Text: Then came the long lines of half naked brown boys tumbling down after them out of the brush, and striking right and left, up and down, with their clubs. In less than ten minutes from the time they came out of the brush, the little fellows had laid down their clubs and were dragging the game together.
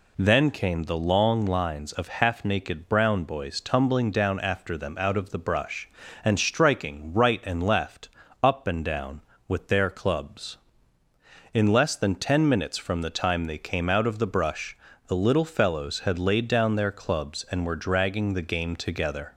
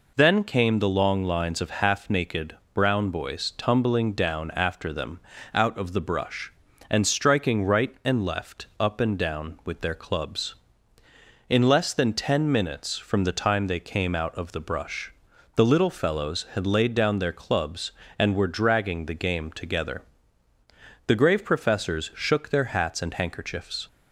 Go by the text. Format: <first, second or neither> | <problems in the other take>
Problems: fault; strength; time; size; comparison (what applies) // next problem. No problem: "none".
first | pauses between "naked" and "brown"; slight; at 2.5 s; 0.20 s long // pauses between "them" and "out"; slight; at 5.1 s; 0.36 s long // goes on to say "The grave professors shook their hats and handkerchiefs"; strong; from 21.0 s on; 2.8 s long